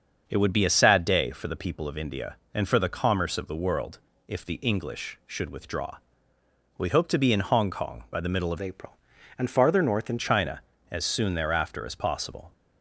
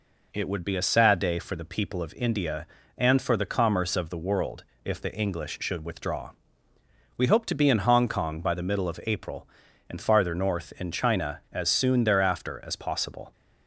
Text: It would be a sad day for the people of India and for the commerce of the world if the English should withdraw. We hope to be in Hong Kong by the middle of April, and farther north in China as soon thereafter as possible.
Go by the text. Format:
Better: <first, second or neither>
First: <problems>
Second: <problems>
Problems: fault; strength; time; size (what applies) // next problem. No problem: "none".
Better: second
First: starts louder than the rest; until 1.2 s; 6.5 dB // pauses between "world" and "if"; slight; at 3.9 s; 0.28 s long // changes voice from "April" to "in"; from 8.6 to 10.1 s; 1.5 s long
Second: pauses between "world" and "if"; slight; at 4.6 s; 0.22 s long